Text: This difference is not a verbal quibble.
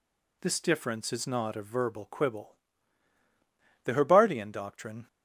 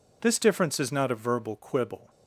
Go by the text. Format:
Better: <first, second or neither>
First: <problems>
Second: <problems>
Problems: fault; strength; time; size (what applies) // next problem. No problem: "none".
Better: second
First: goes on to say "The Herbartian doctrine"; noticeable; from 3.8 s on; 1.2 s long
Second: none